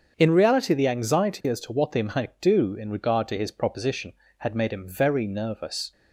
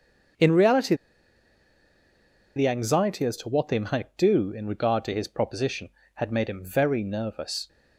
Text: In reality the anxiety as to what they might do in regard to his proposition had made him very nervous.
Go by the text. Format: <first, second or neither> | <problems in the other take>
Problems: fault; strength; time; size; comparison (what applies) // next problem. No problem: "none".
first | starts louder than the rest; strong; until 2.9 s; 7 dB; also in the first // pauses between "reality" and "the"; strong; at 0.9 s; 1.6 s long